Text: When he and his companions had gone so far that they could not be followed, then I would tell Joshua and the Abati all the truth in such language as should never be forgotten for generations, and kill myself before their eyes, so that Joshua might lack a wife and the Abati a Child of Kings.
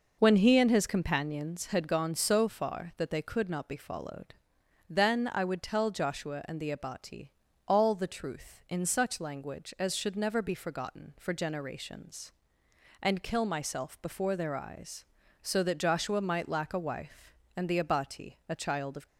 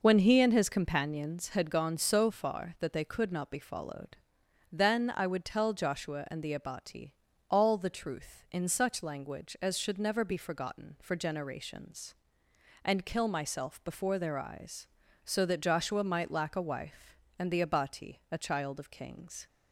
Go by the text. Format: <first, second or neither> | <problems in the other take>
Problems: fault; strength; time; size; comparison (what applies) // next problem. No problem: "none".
second | pauses between "Abati" and "all"; at 7.3 s; 0.38 s long; also in the second // stops before "Kings"; at 19.0 s